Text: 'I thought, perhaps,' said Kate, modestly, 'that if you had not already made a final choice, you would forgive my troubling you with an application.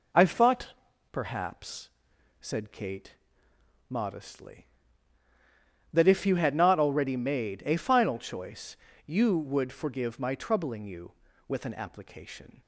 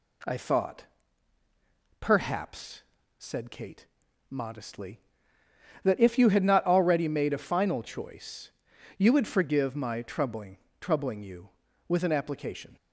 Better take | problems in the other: first | says "troubling" twice; at 10.7 s

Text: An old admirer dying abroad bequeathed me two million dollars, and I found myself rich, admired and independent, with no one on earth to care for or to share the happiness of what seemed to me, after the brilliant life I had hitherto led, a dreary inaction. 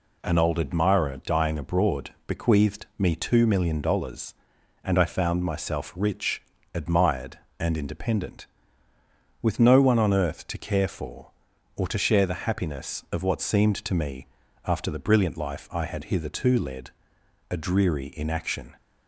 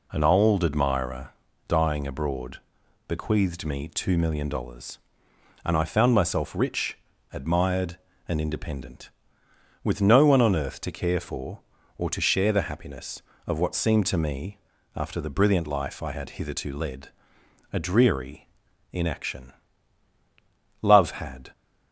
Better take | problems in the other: first | pauses between "admirer" and "dying"; at 1.2 s; 0.38 s long // pauses between "abroad" and "bequeathed"; noticeable; at 2.5 s; 0.48 s long; slight in the first // pauses between "dreary" and "inaction"; at 18.4 s; 0.44 s long // goes on to say "Love had"; noticeable; from 20.8 s on; 0.70 s long

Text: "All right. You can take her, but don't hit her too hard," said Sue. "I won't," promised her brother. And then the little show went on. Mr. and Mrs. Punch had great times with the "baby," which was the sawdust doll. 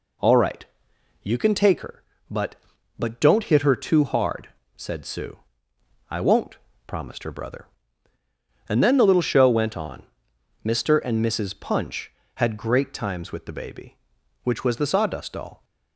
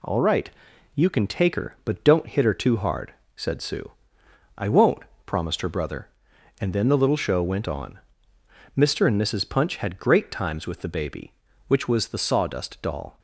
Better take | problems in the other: second | says "but" twice; at 2.9 s

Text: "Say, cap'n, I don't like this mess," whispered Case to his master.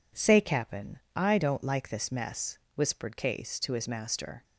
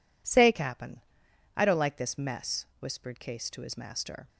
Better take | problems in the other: neither | none

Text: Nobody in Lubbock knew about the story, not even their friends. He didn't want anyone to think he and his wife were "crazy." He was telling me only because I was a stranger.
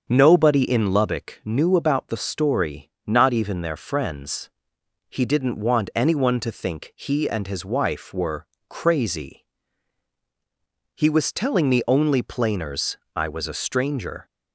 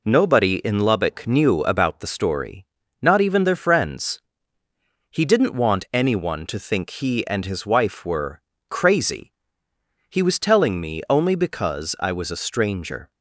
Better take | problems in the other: second | starts louder than the rest; until 1.0 s; 6.5 dB // pauses between "were" and "crazy"; slight; at 8.4 s; 0.24 s long; slight in the second // says "planers" for "because"; at 12.2 s

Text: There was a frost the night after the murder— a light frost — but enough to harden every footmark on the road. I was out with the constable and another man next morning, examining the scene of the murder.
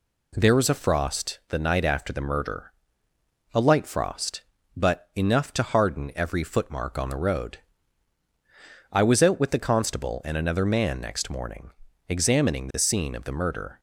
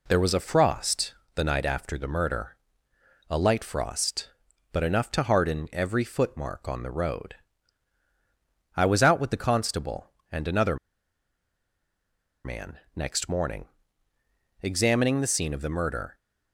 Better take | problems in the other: first | pauses between "frost" and "the"; slight; at 1.1 s; 0.20 s long // pauses between "another" and "man"; strong; at 10.7 s; 1.6 s long // pauses between "man" and "next"; slight; at 12.7 s; 0.18 s long

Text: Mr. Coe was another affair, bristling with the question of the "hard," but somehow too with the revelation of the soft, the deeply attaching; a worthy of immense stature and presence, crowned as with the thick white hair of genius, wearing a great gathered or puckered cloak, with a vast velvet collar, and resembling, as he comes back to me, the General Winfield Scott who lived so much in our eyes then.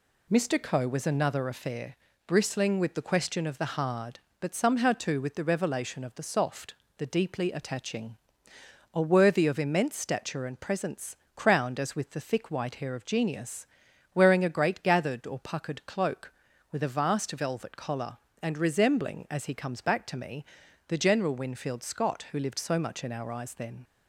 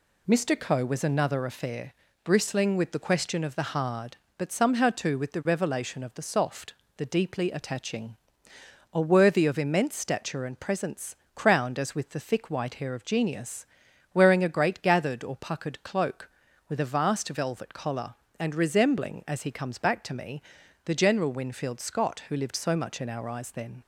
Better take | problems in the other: neither | none

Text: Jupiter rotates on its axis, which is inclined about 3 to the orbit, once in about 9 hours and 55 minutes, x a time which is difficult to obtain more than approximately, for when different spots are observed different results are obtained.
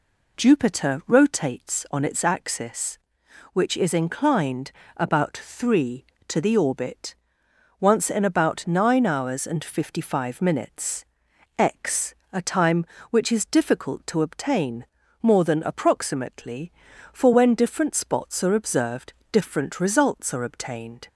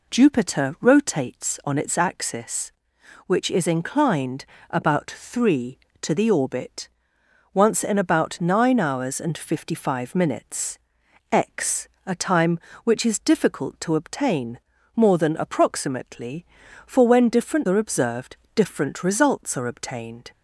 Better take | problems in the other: first | pauses between "inclined" and "about"; slight; at 4.4 s; 0.24 s long; slight in the first // pauses between "x" and "a"; slight; at 11.8 s; 0.18 s long; slight in the first // pauses between "obtain" and "more"; slight; at 14.5 s; 0.34 s long; slight in the first // skips "spots"; at 17.6 s // pauses between "observed" and "different"; slight; at 18.3 s; 0.20 s long; slight in the first

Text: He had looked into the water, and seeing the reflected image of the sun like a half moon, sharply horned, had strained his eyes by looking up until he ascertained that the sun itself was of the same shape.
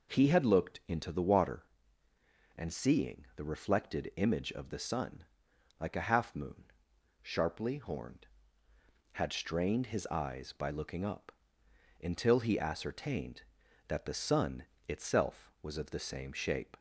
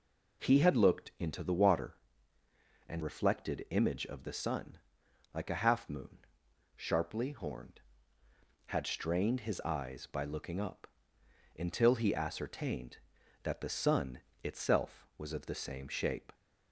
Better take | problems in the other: first | skips "seeing the"; at 3.0 s // pauses between "sun" and "like"; noticeable; at 4.7 s; 0.56 s long; noticeable in the first // pauses between "up" and "until"; noticeable; at 10.8 s; 0.72 s long; noticeable in the first // pauses between "sun" and "itself"; slight; at 14.1 s; 0.24 s long; slight in the first

